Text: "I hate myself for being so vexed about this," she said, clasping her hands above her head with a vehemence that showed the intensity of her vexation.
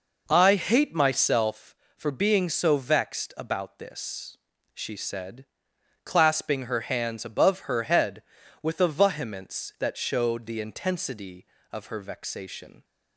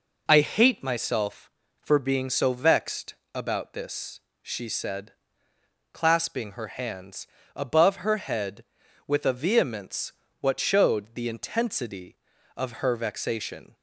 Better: first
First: none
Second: pauses between "vexed" and "about"; slight; at 3.1 s; 0.18 s long // pauses between "hands" and "above"; slight; at 7.2 s; 0.28 s long // says "what" for "that"; at 10.4 s

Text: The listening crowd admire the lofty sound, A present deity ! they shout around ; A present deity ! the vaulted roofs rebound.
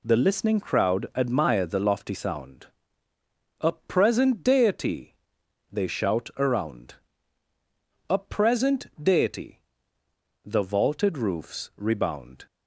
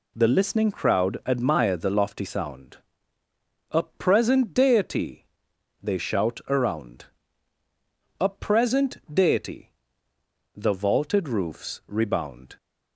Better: neither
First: pauses between "present" and "deity"; slight; at 8.8 s; 0.16 s long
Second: pauses between "present" and "deity"; slight; at 8.9 s; 0.16 s long

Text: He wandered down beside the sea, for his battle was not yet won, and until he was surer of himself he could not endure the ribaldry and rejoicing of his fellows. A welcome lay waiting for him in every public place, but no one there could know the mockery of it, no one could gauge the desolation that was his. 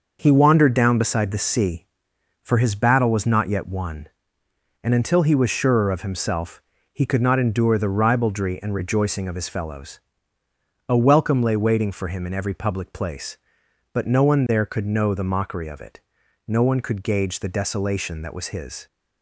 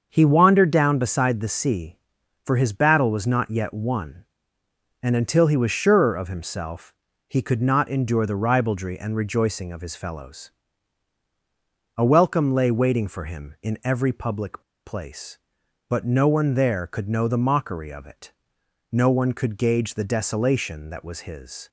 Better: first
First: starts louder than the rest; noticeable; until 1.2 s; 6 dB // pauses between "himself" and "he"; slight; at 6.6 s; 0.32 s long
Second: starts louder than the rest; until 1.1 s; 6.5 dB // pauses between "himself" and "he"; slight; at 6.9 s; 0.36 s long // pauses between "public" and "place"; slight; at 14.6 s; 0.23 s long

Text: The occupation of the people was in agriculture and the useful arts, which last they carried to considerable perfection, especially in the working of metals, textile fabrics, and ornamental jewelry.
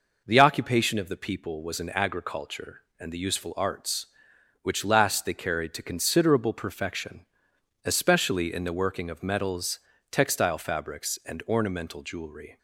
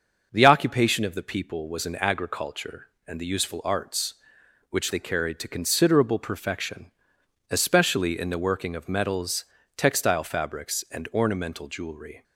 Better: first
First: none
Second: starts louder than the rest; until 1.3 s; 6.5 dB // skips "last"; at 4.9 s

